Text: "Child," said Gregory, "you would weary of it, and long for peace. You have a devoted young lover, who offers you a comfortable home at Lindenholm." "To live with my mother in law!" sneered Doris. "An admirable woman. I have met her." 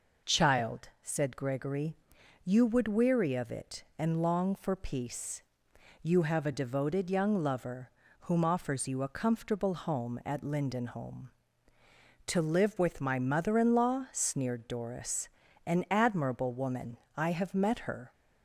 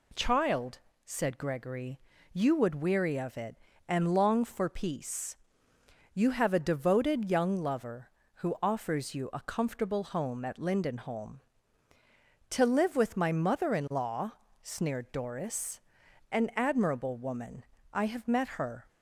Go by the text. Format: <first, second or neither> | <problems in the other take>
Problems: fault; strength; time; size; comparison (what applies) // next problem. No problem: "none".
second | says "whom" for "who"; at 8.1 s